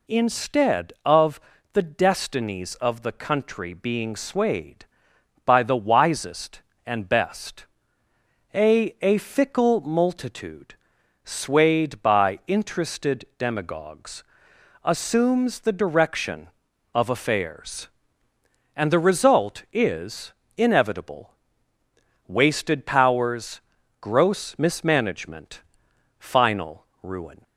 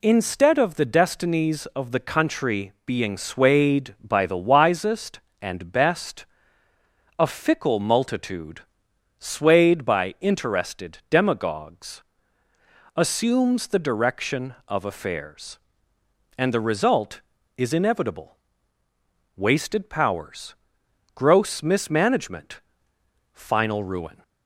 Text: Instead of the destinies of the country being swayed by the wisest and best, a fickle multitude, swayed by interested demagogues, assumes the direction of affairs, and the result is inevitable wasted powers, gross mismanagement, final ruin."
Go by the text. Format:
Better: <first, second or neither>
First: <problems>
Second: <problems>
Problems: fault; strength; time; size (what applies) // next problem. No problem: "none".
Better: second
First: pauses between "of" and "the"; slight; at 1.3 s; 0.34 s long // says "a" twice; at 9.0 s // pauses between "is" and "inevitable"; slight; at 20.3 s; 0.24 s long // pauses between "inevitable" and "wasted"; noticeable; at 21.3 s; 0.96 s long // pauses between "final" and "ruin"; slight; at 26.8 s; 0.18 s long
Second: pauses between "inevitable" and "wasted"; at 18.3 s; 1.0 s long